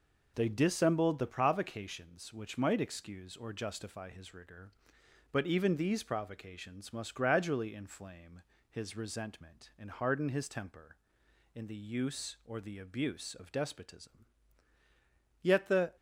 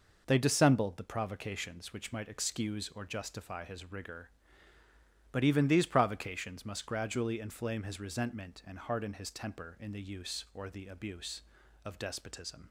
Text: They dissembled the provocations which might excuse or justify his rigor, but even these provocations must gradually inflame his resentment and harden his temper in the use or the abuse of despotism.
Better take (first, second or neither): second